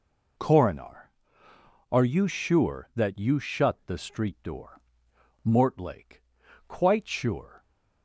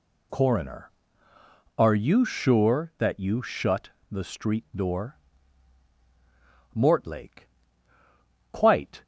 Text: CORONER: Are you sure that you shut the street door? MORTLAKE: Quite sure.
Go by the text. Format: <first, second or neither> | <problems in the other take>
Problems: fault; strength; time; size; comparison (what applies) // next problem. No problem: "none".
first | pauses between "shut" and "the"; slight; at 3.8 s; 0.20 s long // stops before "sure"; at 9.0 s